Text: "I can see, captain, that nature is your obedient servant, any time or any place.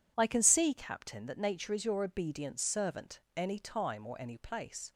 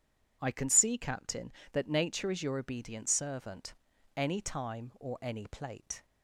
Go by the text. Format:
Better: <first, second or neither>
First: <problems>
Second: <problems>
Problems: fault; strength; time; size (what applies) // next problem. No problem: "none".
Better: first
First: none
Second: says "plate" for "place"; at 5.4 s